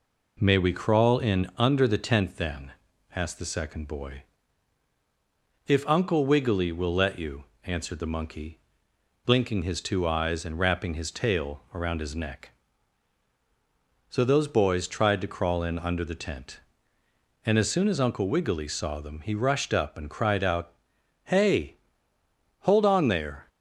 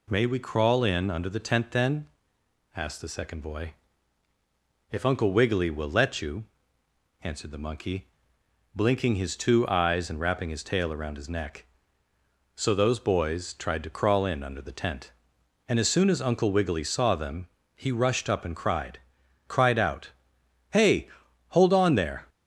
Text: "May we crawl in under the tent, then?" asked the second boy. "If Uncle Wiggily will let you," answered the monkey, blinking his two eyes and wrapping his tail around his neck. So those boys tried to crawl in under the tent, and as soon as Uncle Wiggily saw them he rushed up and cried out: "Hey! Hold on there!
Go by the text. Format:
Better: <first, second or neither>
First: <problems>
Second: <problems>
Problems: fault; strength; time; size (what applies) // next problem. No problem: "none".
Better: first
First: none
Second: pauses between "them" and "he"; slight; at 17.4 s; 0.28 s long // says "cried" twice; at 19.4 s